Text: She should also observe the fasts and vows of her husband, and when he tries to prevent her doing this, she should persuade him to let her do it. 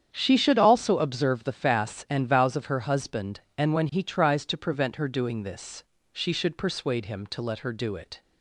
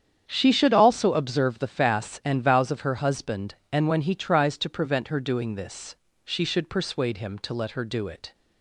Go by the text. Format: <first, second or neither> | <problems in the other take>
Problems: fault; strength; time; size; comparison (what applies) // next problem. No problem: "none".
neither | starts louder than the rest; strong; the same in both